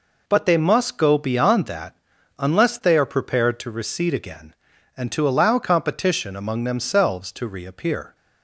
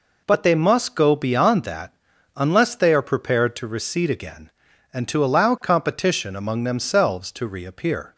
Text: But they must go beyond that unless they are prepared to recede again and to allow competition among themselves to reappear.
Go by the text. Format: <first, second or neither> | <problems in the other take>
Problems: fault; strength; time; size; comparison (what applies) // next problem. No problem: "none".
neither | pauses between "that" and "unless"; the same in both